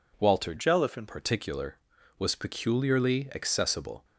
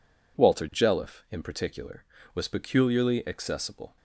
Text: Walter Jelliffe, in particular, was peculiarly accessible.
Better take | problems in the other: second | changes voice from "Jelliffe" to "in"; from 0.5 to 1.0 s; 0.5 s long

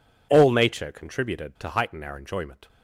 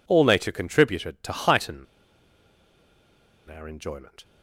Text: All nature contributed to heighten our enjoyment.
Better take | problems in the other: first | pauses between "heighten" and "our"; strong; at 1.8 s; 1.6 s long

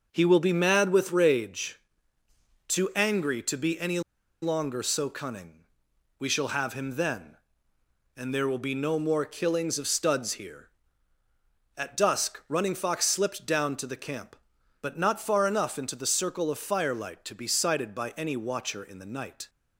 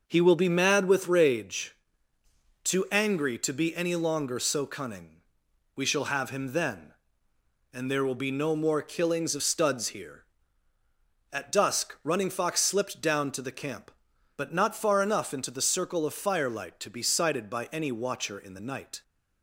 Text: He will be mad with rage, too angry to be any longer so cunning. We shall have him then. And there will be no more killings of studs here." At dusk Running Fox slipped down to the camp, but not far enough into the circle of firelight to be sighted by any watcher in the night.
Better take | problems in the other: second | pauses between "any" and "longer"; at 3.9 s; 0.42 s long

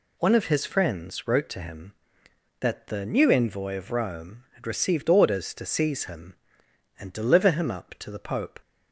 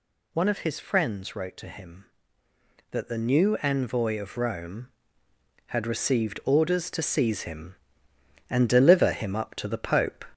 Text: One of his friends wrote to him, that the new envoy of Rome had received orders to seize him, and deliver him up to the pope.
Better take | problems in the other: first | gets louder; throughout; 3.5 dB

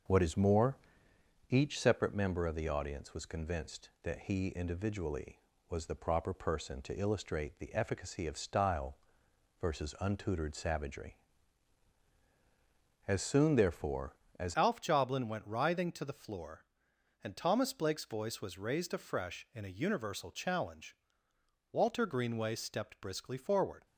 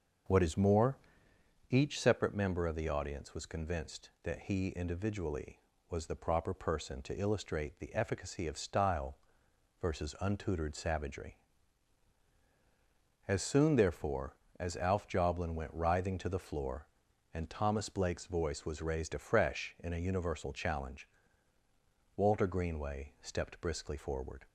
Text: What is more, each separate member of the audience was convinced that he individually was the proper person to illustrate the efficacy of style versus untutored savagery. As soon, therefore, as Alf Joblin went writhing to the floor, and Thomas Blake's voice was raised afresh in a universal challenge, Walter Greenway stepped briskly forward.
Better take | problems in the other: second | pauses between "style" and "versus"; noticeable; at 8.9 s; 0.64 s long; noticeable in the second // changes voice at "Alf"; from 14.5 s on; 9.3 s long

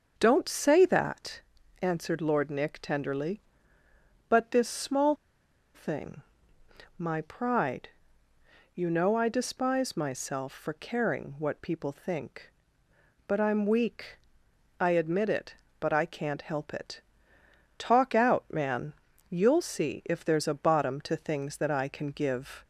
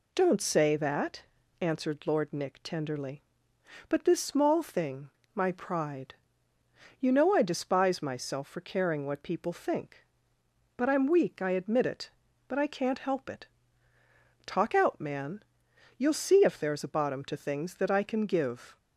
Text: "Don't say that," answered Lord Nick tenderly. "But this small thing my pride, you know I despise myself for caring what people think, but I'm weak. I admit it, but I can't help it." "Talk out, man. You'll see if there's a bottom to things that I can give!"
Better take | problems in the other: second | starts louder than the rest; until 1.1 s; 6.5 dB // pauses between "small" and "thing"; noticeable; at 5.1 s; 0.60 s long // pauses between "thing" and "my"; noticeable; at 6.2 s; 0.76 s long; slight in the second

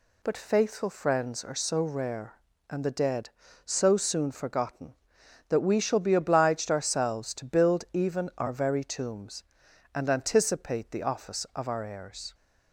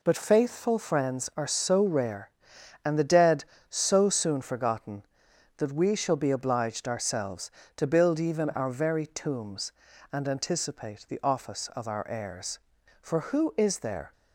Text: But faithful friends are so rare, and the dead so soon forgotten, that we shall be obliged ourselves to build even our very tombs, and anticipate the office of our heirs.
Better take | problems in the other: first | goes on to say "For who is there"; noticeable; from 13.0 s on; 1.1 s long

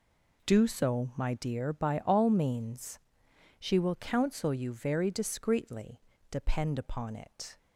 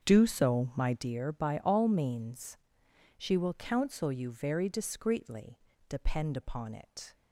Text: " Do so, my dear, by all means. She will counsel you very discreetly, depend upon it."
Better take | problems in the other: first | starts louder than the rest; strong; until 1.1 s; 7 dB

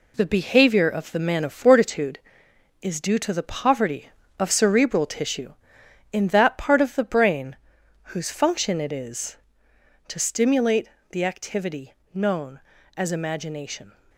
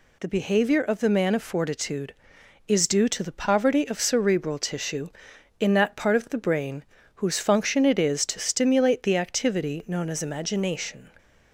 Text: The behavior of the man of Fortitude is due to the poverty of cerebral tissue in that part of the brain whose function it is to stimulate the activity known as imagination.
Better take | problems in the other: second | gets quieter; noticeable; throughout; 6 dB // pauses between "brain" and "whose"; noticeable; at 7.5 s; 0.56 s long; slight in the second // pauses between "stimulate" and "the"; slight; at 10.8 s; 0.24 s long // pauses between "activity" and "known"; slight; at 11.9 s; 0.20 s long

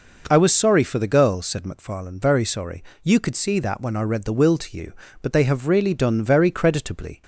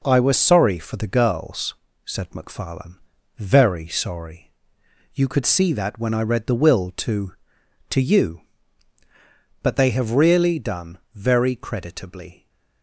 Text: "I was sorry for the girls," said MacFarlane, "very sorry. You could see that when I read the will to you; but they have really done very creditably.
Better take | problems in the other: first | says "to" twice; at 7.9 s // pauses between "done" and "very"; slight; at 10.9 s; 0.16 s long

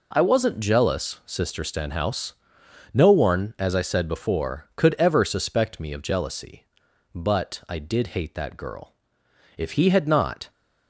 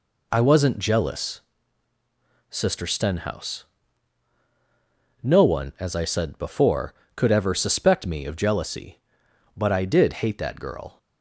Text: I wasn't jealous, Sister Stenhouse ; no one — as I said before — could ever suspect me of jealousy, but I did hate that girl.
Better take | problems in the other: second | goes on to say "If he had not"; noticeable; from 9.5 s on; 0.94 s long

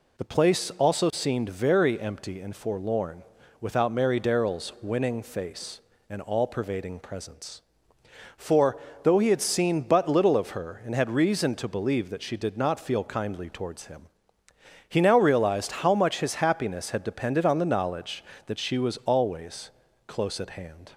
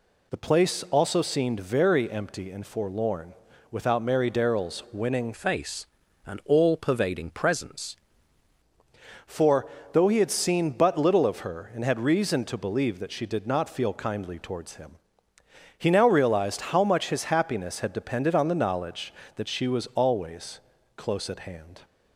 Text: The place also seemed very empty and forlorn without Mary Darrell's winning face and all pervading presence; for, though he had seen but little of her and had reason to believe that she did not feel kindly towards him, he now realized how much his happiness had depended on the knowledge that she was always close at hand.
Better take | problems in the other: first | pauses between "forlorn" and "without"; slight; at 3.3 s; 0.36 s long; slight in the first // changes voice from "face" to "presence"; from 5.3 to 7.9 s; 2.6 s long // pauses between "always" and "close"; at 20.5 s; 0.38 s long; also in the first

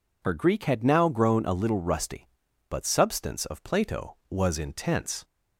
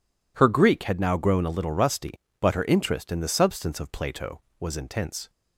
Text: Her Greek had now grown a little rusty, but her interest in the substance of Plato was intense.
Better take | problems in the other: second | skips "her interest in the"; at 2.8 s

